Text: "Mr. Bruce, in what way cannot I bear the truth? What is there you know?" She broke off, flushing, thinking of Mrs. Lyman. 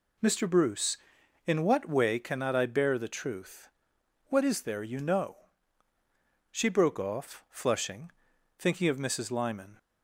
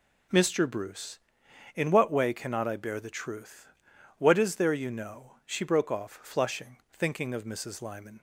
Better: neither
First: none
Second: none

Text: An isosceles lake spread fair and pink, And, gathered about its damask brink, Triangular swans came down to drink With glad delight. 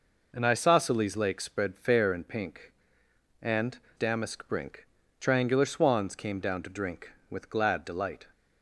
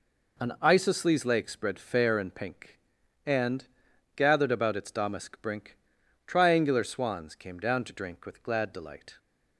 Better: second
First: skips "gathered about its"; at 3.8 s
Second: none

